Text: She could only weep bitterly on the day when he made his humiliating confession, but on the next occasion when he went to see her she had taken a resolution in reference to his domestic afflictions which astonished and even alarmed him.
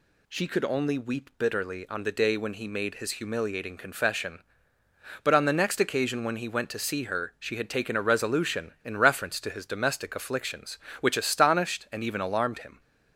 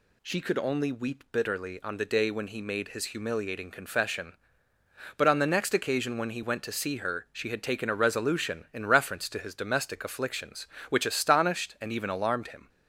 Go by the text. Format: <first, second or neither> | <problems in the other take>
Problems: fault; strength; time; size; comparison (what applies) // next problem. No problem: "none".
neither | none